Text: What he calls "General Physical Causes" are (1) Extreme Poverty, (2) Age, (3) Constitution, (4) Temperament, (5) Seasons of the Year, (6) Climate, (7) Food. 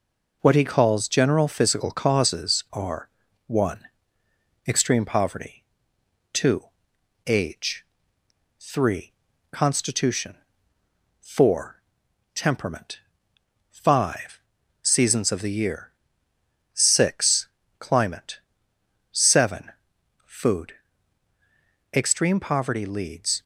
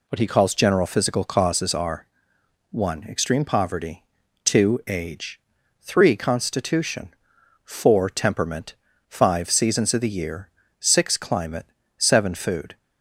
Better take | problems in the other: second | goes on to say "Extreme poverty leads"; from 21.9 s on; 1.5 s long

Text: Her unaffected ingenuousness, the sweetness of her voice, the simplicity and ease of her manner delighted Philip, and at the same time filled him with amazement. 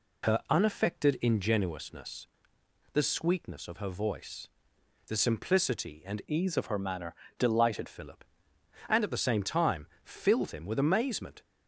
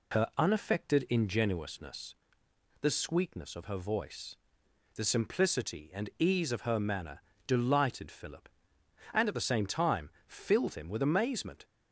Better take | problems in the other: second | changes voice from "ease" to "delighted"; from 6.2 to 7.8 s; 1.6 s long // pauses between "manner" and "delighted"; slight; at 7.1 s; 0.24 s long; slight in the second // pauses between "time" and "filled"; slight; at 9.8 s; 0.16 s long; slight in the second

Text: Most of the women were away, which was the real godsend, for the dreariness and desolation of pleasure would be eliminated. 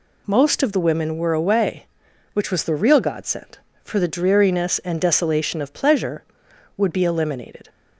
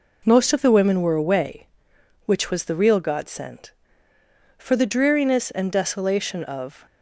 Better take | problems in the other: first | stops before "pleasure would be eliminated"; at 6.8 s

